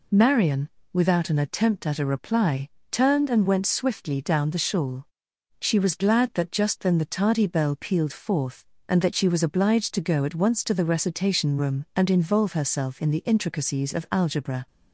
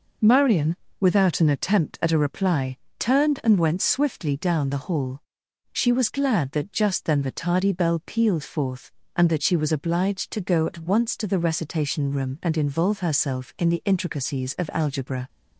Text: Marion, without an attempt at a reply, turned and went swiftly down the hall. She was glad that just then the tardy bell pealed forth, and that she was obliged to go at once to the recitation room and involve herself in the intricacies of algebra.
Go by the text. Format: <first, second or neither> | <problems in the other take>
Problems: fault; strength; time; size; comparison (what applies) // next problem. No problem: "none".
second | says "shawl" for "hall"; at 4.5 s